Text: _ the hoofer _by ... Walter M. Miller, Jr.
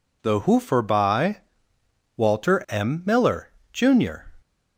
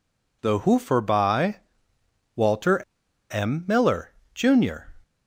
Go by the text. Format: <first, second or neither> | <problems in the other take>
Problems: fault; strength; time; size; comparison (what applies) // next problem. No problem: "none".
first | pauses between "Walter" and "M"; noticeable; at 2.8 s; 0.52 s long